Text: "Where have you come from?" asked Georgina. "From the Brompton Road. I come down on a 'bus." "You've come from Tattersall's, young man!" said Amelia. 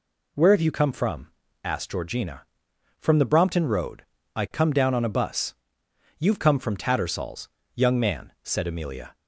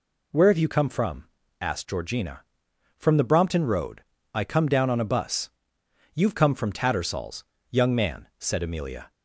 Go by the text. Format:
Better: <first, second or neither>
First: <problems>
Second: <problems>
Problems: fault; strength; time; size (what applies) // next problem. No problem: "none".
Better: neither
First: none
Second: none